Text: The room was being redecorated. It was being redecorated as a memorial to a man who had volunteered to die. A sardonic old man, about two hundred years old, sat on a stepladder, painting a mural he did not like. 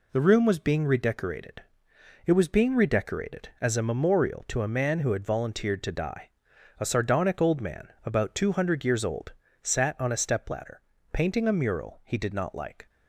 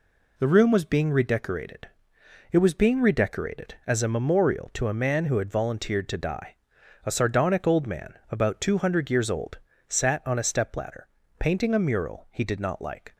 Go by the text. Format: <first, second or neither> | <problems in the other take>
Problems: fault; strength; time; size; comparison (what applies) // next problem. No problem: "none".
neither | none